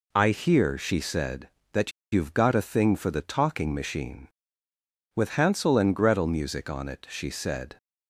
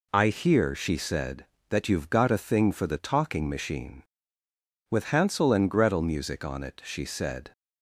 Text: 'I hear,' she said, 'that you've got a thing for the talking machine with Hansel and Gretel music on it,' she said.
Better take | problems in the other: second | pauses between "that" and "you've"; slight; at 1.9 s; 0.21 s long

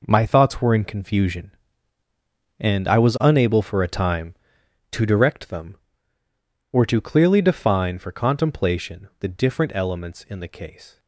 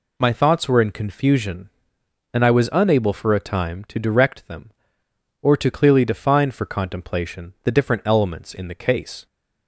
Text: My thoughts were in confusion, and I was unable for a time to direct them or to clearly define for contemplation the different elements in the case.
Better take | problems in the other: second | gets quieter; strong; throughout; 10 dB

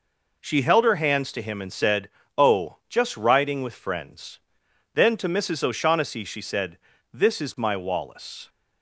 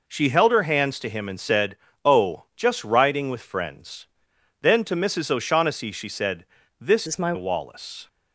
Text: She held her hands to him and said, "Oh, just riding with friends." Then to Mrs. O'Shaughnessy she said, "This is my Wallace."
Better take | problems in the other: first | changes voice from "is" to "my"; from 7.0 to 7.3 s; 0.3 s long

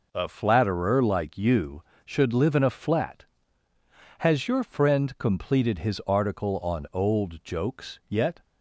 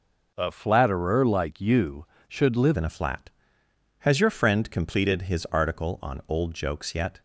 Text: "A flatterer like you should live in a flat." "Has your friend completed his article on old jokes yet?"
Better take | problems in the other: first | changes voice at "in"; from 2.7 s on; 4.5 s long

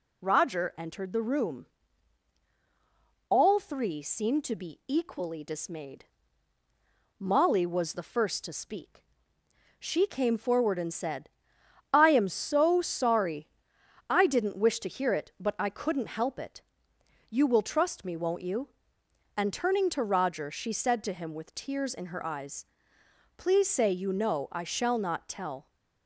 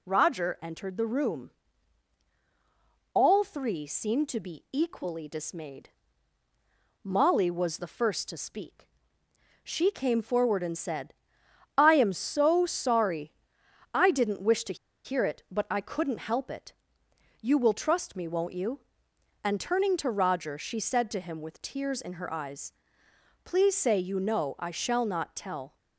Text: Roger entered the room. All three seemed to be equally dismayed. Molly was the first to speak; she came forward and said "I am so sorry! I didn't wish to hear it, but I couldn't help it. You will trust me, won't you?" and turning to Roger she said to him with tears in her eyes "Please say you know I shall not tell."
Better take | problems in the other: first | pauses between "said" and "I"; noticeable; at 11.1 s; 0.64 s long; noticeable in the first // pauses between "to" and "hear"; slight; at 14.7 s; 0.27 s long // pauses between "eyes" and "Please"; noticeable; at 22.7 s; 0.72 s long; noticeable in the first

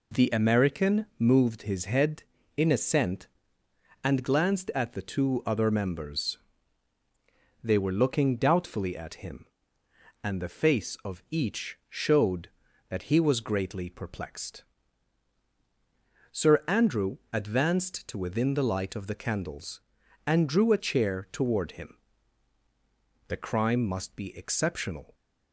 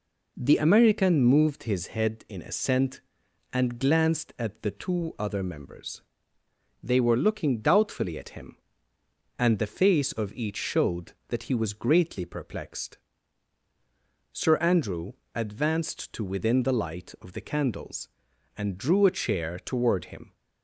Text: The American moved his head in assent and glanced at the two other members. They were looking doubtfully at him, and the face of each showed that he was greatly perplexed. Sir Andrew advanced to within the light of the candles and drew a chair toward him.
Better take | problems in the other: second | pauses between "Andrew" and "advanced"; slight; at 17.1 s; 0.16 s long; slight in the second // goes on to say "The crime must be exceptional"; strong; from 23.2 s on; 1.8 s long

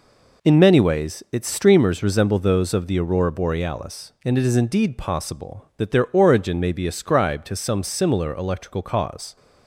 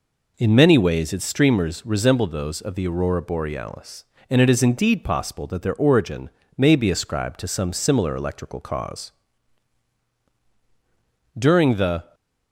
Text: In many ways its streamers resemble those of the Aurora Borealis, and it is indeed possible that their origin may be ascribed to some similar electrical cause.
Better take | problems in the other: first | pauses between "origin" and "may"; slight; at 6.2 s; 0.30 s long // goes on to say "During the"; noticeable; from 11.3 s on; 0.76 s long

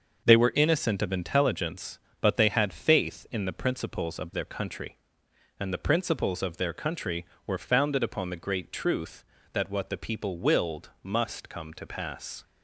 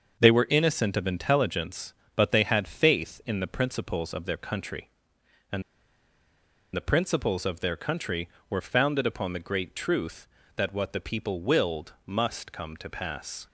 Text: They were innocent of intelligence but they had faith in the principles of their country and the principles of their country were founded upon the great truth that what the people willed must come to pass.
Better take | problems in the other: first | starts louder than the rest; until 1.2 s; 6.5 dB; also in the first // pauses between "and" and "the"; at 5.6 s; 1.1 s long

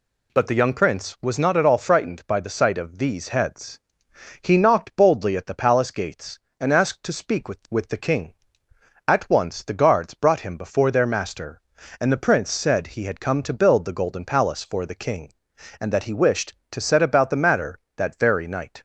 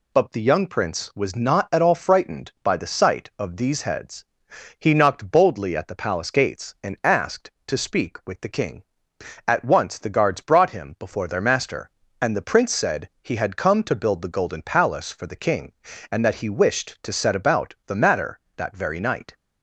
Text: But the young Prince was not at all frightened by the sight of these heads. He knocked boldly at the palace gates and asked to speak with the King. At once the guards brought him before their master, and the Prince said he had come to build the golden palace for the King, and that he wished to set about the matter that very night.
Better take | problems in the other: second | says "with" twice; at 7.6 s

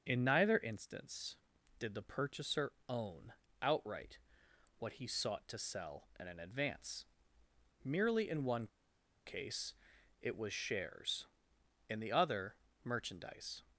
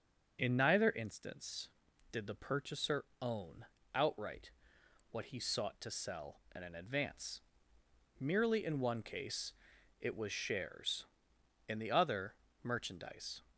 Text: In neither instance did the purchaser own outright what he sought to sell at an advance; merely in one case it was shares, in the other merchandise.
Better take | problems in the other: second | pauses between "purchaser" and "own"; slight; at 2.7 s; 0.16 s long; slight in the second // pauses between "own" and "outright"; slight; at 3.3 s; 0.28 s long; slight in the second // pauses between "outright" and "what"; noticeable; at 4.1 s; 0.60 s long; noticeable in the second // pauses between "one" and "case"; noticeable; at 8.6 s; 0.58 s long // pauses between "case" and "it"; noticeable; at 9.7 s; 0.48 s long; noticeable in the second // pauses between "other" and "merchandise"; slight; at 12.5 s; 0.26 s long; slight in the second

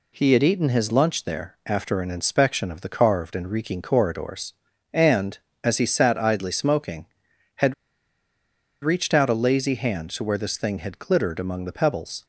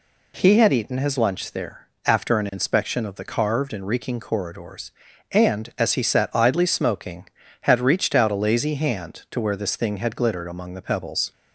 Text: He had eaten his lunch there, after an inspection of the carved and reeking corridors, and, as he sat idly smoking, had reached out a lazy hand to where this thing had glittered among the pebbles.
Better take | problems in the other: second | pauses between "had" and "reached"; at 7.7 s; 1.0 s long

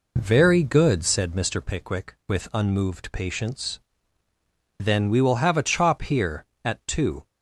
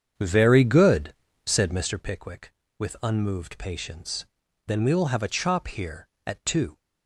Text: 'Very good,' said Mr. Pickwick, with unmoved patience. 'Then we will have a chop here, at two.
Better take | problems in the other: first | starts louder than the rest; strong; until 2.1 s; 7.5 dB

